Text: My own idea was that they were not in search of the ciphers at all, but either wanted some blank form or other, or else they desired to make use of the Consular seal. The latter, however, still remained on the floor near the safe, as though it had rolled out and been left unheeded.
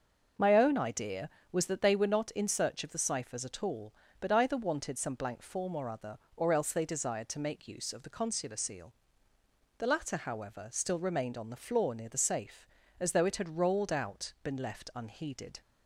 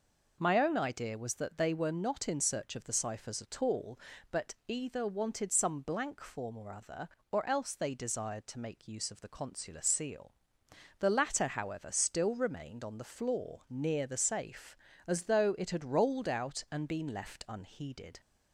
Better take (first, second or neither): second